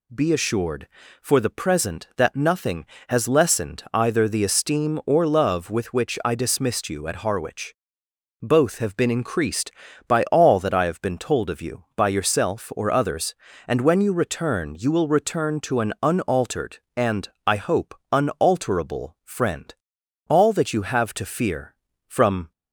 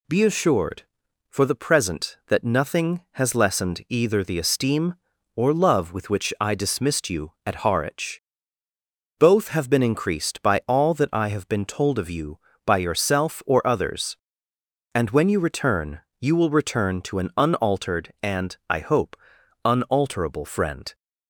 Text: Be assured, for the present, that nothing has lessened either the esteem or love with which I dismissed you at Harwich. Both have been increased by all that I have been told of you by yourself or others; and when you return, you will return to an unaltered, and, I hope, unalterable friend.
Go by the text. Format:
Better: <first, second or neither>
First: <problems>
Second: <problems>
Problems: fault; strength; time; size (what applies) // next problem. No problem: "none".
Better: second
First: goes on to say "All that you have to fear from"; strong; from 20.2 s on; 2.2 s long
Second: none